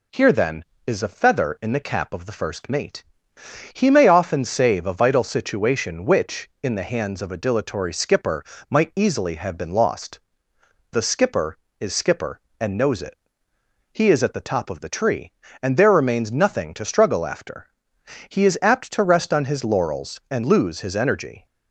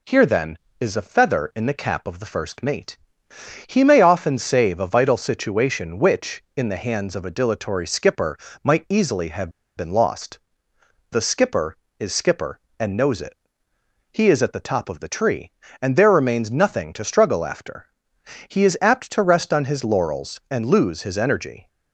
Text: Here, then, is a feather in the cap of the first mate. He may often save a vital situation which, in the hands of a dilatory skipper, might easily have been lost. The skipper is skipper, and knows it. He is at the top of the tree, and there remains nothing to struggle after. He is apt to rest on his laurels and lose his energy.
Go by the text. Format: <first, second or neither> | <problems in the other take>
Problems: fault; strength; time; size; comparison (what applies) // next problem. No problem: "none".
first | pauses between "have" and "been"; slight; at 9.4 s; 0.27 s long